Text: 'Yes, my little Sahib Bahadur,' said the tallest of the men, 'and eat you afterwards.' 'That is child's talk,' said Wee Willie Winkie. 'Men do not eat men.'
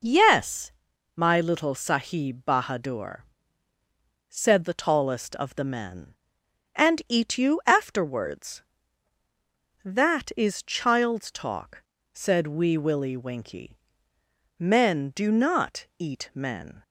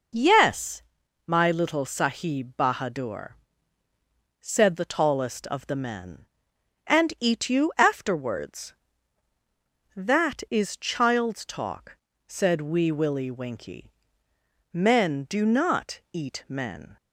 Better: neither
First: none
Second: none

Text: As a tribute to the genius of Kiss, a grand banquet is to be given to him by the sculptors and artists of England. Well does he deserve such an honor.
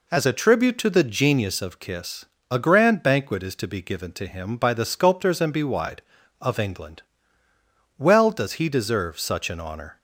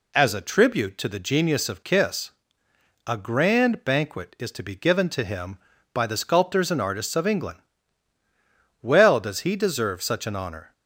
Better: second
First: says "bewide" for "artists"; at 5.5 s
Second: none

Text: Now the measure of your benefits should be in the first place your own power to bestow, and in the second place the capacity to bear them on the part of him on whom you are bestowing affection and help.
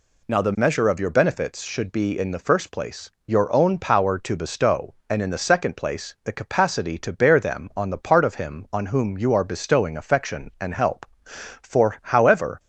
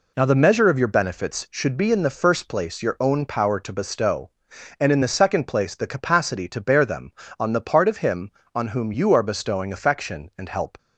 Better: second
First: pauses between "place" and "your"; slight; at 3.1 s; 0.16 s long // goes on to say "For however"; noticeable; from 11.6 s on; 0.98 s long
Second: none

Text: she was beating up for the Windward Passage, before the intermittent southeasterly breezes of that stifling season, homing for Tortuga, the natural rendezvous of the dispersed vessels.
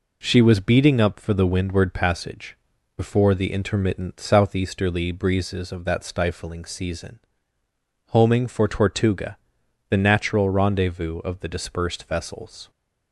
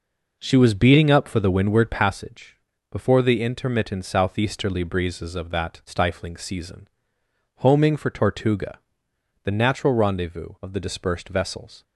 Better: neither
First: none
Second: none

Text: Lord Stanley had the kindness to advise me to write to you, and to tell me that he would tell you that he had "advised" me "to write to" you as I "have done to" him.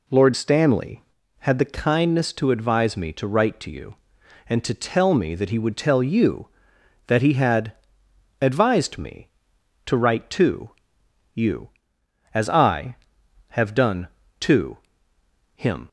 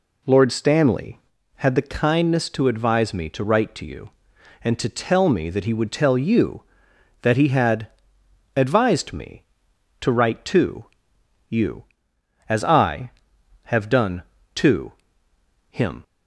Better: neither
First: pauses between "had" and "advised"; noticeable; at 7.7 s; 0.68 s long // pauses between "to" and "you"; noticeable; at 10.6 s; 0.64 s long // pauses between "to" and "him"; noticeable; at 14.7 s; 0.78 s long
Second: pauses between "had" and "advised"; noticeable; at 7.8 s; 0.68 s long // pauses between "to" and "you"; noticeable; at 10.8 s; 0.64 s long // pauses between "to" and "him"; noticeable; at 14.9 s; 0.78 s long

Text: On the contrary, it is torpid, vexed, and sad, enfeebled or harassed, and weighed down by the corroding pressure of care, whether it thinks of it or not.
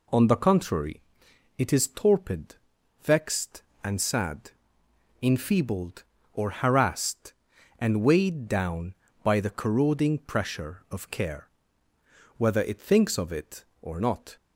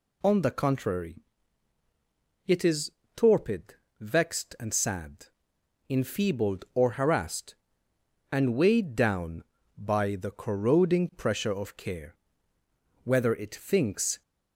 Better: first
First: none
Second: pauses between "is" and "torpid"; slight; at 2.9 s; 0.24 s long // stops before "of it or not"; at 14.2 s

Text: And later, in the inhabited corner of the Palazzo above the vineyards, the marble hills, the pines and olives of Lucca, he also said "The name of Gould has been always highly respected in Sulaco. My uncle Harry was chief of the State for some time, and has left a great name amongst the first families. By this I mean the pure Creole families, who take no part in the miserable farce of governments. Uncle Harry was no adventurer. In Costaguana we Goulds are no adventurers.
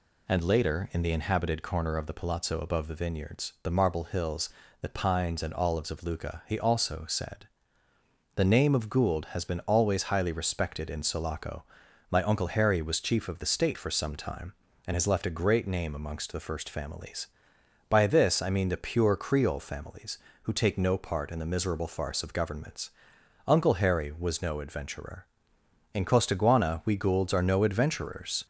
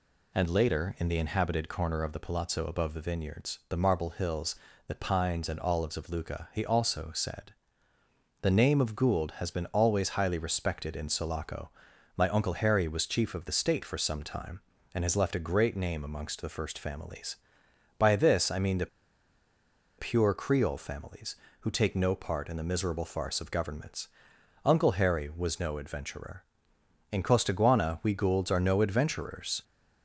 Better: first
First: pauses between "said" and "The"; noticeable; at 7.4 s; 0.88 s long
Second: pauses between "said" and "The"; noticeable; at 7.5 s; 0.88 s long // pauses between "the" and "pure"; at 18.8 s; 1.1 s long

